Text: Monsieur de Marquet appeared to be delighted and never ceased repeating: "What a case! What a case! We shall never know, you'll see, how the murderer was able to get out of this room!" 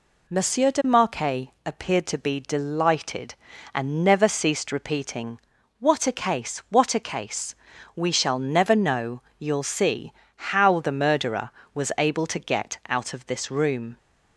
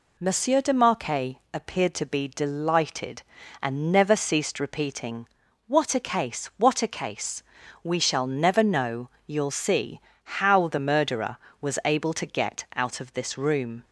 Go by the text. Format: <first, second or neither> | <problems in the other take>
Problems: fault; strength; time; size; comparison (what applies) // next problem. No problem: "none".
neither | pauses between "Marquet" and "appeared"; slight; the same in both